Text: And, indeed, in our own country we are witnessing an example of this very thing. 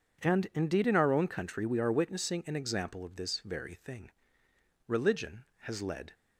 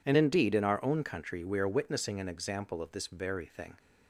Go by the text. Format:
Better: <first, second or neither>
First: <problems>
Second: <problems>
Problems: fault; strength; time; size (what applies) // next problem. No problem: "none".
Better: second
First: goes on to say "Religion has led"; noticeable; from 4.8 s on; 1.2 s long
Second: none